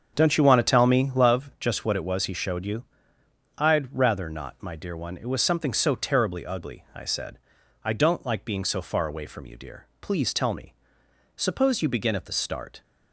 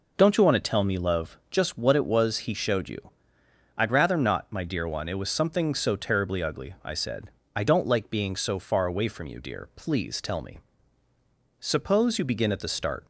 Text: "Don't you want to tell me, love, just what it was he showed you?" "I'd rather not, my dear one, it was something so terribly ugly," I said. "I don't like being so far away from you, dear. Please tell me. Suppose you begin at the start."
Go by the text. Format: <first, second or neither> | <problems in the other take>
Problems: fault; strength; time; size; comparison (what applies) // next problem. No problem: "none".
second | starts louder than the rest; strong; until 1.3 s; 7 dB